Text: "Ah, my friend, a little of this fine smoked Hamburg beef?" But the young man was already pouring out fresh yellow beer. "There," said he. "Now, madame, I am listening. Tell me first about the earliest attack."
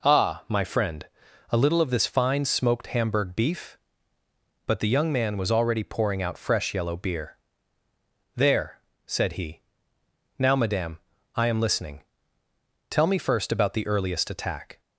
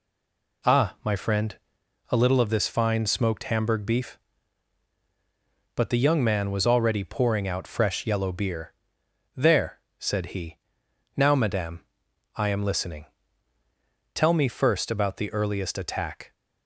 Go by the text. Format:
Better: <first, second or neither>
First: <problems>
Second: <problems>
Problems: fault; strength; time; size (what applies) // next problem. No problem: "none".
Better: first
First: none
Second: stays silent before the first word; slight; until 0.6 s; 0.6 s long